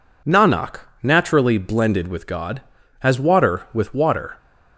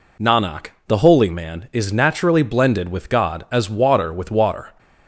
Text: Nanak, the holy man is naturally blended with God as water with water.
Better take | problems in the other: second | skips "the holy man is"; at 0.8 s

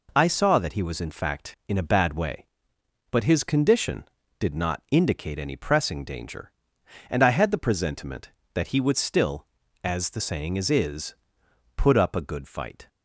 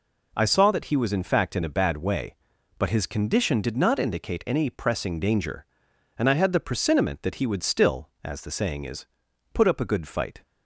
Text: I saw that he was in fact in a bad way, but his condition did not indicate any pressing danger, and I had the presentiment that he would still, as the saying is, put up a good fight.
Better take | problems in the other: second | says "is" twice; at 10.6 s

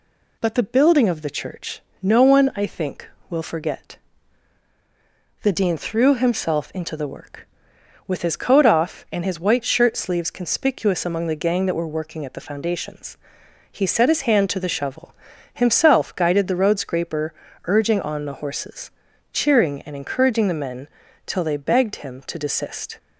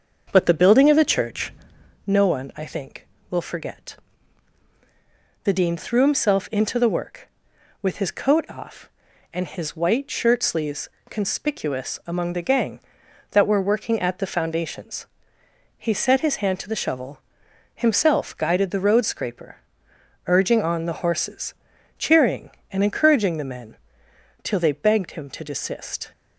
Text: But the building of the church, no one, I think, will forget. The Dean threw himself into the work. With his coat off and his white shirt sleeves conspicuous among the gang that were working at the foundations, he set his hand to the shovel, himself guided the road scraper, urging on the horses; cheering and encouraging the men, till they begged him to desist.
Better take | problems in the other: first | starts louder than the rest; until 2.0 s; 6.5 dB // pauses between "sleeves" and "conspicuous"; slight; at 10.8 s; 0.20 s long

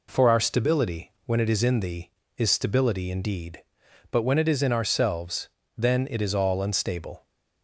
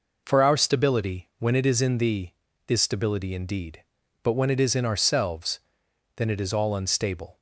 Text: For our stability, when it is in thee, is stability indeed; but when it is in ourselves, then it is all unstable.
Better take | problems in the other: neither | none

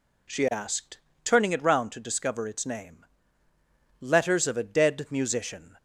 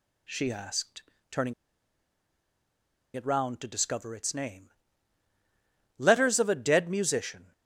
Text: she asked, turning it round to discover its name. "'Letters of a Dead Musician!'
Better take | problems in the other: first | pauses between "turning" and "it"; strong; at 1.5 s; 1.6 s long

